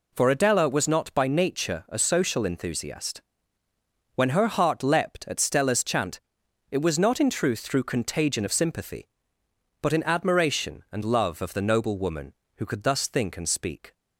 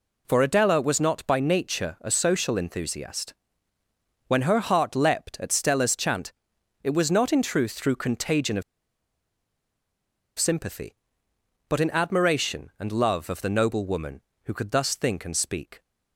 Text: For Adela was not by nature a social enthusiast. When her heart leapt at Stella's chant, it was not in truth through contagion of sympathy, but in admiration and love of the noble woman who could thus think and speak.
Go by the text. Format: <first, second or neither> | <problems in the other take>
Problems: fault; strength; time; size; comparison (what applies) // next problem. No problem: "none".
first | pauses between "of" and "sympathy"; strong; at 8.6 s; 1.7 s long